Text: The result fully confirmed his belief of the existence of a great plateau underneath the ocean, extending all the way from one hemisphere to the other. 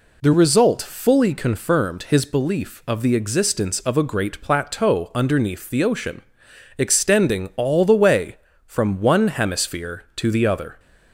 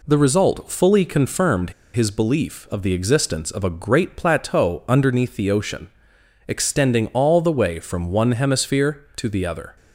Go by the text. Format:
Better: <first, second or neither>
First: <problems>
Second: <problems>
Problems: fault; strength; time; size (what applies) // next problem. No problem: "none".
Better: first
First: none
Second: pauses between "confirmed" and "his"; slight; at 1.7 s; 0.23 s long